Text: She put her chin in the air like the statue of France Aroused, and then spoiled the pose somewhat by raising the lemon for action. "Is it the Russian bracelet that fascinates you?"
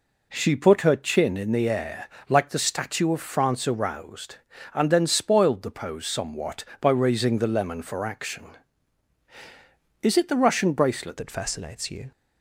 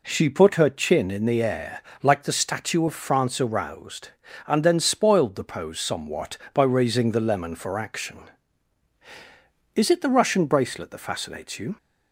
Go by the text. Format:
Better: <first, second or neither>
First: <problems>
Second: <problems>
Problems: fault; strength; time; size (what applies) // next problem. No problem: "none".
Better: second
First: pauses between "air" and "like"; slight; at 2.0 s; 0.20 s long // changes voice at "that"; from 11.1 s on; 1.0 s long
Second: pauses between "air" and "like"; slight; at 1.8 s; 0.20 s long